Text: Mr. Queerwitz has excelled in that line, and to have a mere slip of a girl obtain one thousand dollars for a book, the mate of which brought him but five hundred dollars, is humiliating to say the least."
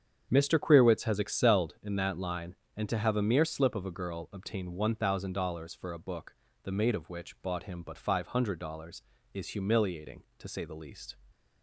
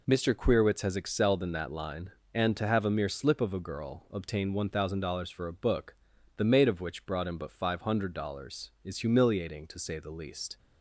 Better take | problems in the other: second | starts louder than the rest; strong; until 1.3 s; 8 dB // says "bought" for "brought"; at 7.4 s // stays silent after the last word; slight; from 11.1 s on; 0.5 s long

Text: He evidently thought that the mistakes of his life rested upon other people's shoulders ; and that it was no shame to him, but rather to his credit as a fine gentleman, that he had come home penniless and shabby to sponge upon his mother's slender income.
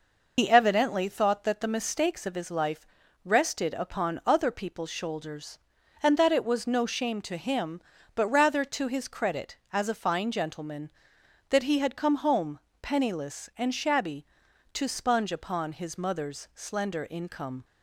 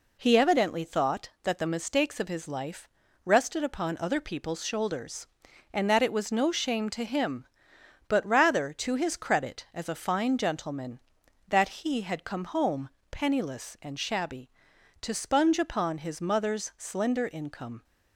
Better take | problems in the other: second | loses the start of "He"; at 0.3 s; 75 ms // pauses between "life" and "rested"; at 2.8 s; 0.40 s long; slight in the second // pauses between "home" and "penniless"; slight; at 12.5 s; 0.24 s long; slight in the second

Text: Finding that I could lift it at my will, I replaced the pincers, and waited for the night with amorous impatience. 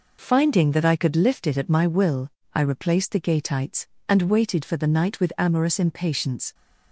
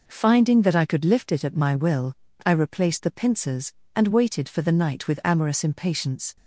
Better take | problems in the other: second | says "gateites" for "pincers"; at 3.1 s

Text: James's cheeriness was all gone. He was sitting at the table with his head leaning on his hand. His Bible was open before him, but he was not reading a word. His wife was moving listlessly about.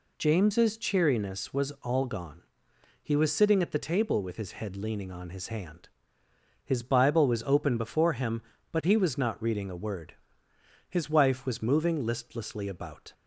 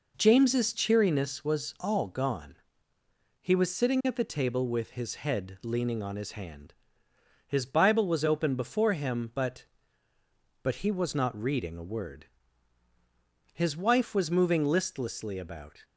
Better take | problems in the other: first | says "but" twice; at 10.6 s

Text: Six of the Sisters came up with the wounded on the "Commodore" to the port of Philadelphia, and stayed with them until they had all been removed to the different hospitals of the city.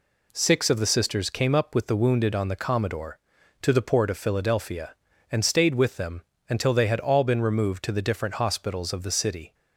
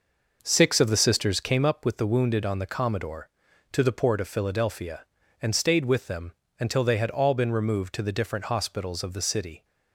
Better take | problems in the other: first | starts louder than the rest; noticeable; until 1.7 s; 5.5 dB // pauses between "them" and "until"; slight; at 6.3 s; 0.26 s long; slight in the first

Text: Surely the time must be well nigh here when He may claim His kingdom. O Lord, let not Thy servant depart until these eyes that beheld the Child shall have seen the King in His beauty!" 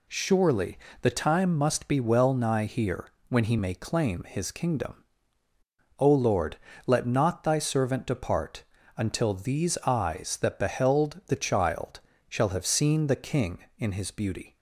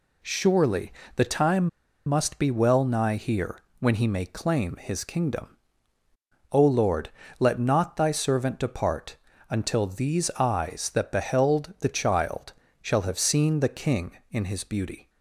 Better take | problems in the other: first | pauses between "Surely" and "the"; slight; at 0.9 s; 0.24 s long; slight in the first // pauses between "time" and "must"; at 1.6 s; 0.37 s long // pauses between "here" and "when"; slight; at 3.5 s; 0.20 s long; slight in the first // pauses between "depart" and "until"; slight; at 9.1 s; 0.34 s long; slight in the first // pauses between "Child" and "shall"; slight; at 12.5 s; 0.30 s long; slight in the first

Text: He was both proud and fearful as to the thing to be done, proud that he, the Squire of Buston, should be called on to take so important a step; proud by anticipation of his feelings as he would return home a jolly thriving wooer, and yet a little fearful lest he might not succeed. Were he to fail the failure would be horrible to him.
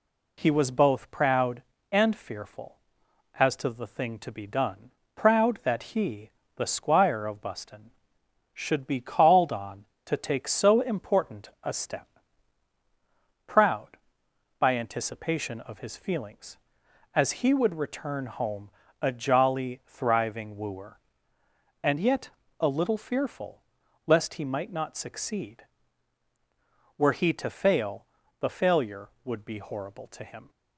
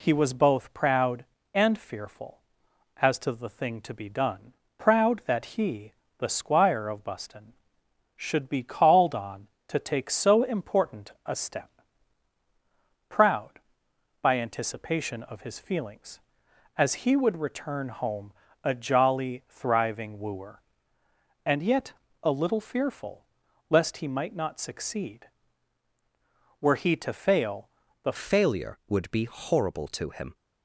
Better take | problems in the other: first | pauses between "important" and "a"; slight; at 11.1 s; 0.16 s long; slight in the first // pauses between "home" and "a"; slight; at 18.3 s; 0.30 s long; slight in the first // pauses between "yet" and "a"; slight; at 21.9 s; 0.30 s long; slight in the first // pauses between "fearful" and "lest"; noticeable; at 23.2 s; 0.46 s long; noticeable in the first // pauses between "fail" and "the"; slight; at 27.6 s; 0.36 s long; slight in the first // changes voice at "failure"; from 28.1 s on; 2.2 s long

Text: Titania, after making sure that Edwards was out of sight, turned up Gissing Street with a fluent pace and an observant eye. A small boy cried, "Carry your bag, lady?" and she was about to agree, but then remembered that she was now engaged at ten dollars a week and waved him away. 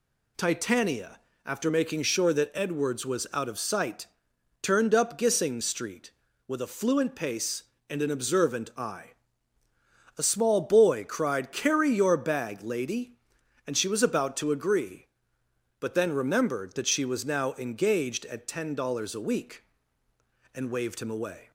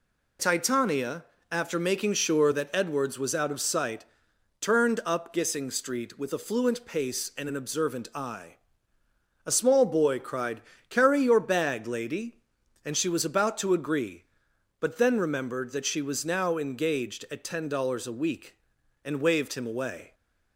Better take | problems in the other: neither | none

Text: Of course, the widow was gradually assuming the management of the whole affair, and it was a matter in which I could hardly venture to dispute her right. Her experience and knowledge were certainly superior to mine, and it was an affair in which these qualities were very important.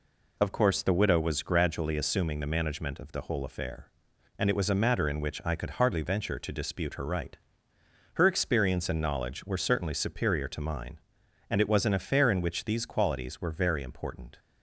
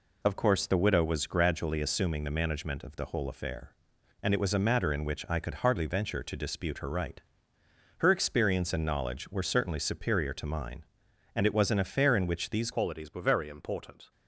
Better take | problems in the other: first | changes voice at "qualities"; from 12.7 s on; 1.4 s long

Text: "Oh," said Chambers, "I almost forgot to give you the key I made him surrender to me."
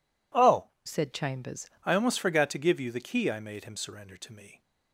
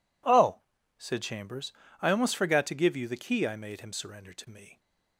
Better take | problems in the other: second | changes voice from "said" to "Chambers"; from 0.8 to 1.6 s; 0.8 s long

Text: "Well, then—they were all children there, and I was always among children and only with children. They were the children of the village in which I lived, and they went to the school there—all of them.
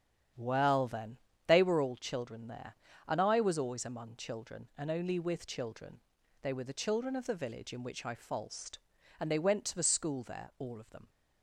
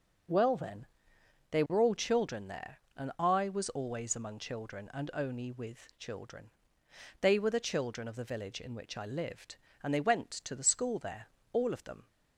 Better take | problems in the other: second | starts louder than the rest; strong; until 1.6 s; 9.5 dB // says "falsed" for "lived"; at 8.1 s

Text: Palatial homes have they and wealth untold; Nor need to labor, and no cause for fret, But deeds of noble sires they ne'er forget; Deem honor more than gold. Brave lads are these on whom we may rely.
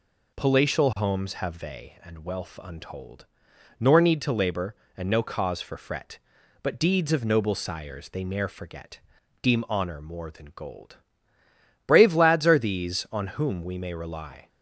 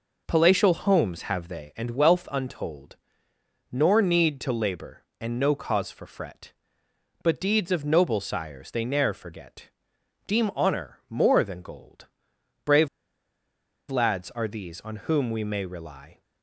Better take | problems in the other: first | pauses between "Brave" and "lads"; at 12.8 s; 1.0 s long

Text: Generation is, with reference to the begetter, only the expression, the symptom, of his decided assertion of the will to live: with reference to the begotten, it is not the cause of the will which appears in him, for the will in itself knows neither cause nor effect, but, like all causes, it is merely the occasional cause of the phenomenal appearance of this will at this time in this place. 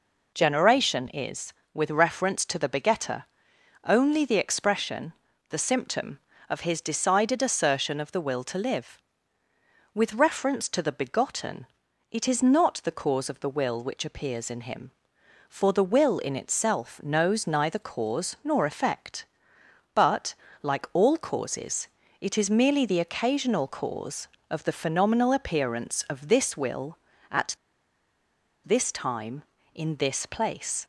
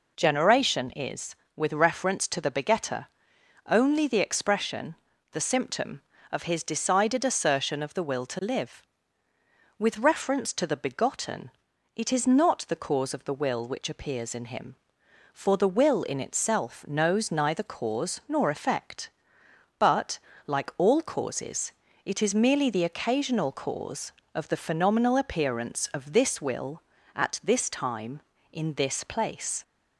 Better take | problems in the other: second | pauses between "at" and "this"; at 27.5 s; 1.0 s long

